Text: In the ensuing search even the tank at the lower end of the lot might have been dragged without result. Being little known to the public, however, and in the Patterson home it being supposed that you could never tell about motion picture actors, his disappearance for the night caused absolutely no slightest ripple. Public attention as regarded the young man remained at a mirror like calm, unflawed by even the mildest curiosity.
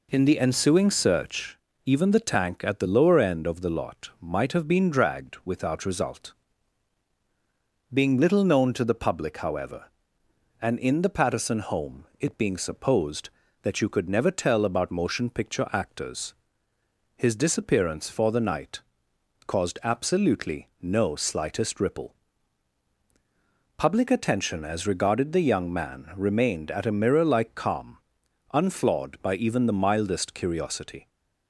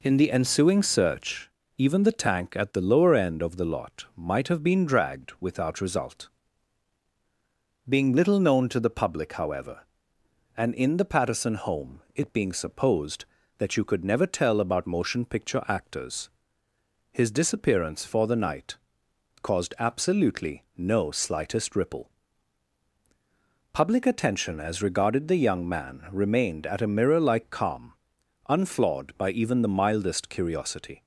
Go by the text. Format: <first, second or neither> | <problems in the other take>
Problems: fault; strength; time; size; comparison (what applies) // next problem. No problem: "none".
neither | pauses between "search" and "even"; slight; the same in both // pauses between "night" and "caused"; noticeable; the same in both